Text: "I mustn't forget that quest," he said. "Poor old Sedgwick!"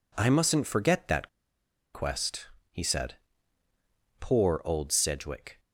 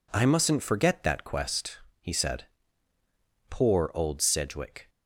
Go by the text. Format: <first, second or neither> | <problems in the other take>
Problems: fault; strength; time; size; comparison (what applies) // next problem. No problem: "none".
second | pauses between "that" and "quest"; noticeable; at 1.2 s; 0.66 s long